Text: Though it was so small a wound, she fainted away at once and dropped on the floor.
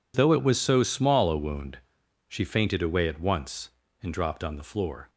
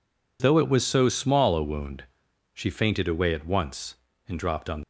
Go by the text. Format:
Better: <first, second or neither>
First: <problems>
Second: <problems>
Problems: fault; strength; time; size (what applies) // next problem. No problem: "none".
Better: first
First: none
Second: stops before "the floor"; at 4.8 s